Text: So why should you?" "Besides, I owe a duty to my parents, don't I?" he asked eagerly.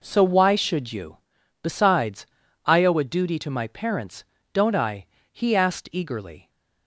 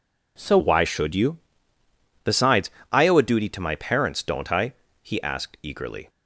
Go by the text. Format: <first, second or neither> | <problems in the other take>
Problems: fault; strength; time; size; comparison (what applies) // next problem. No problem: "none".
first | changes voice at "why"; from 0.5 s on; 5.5 s long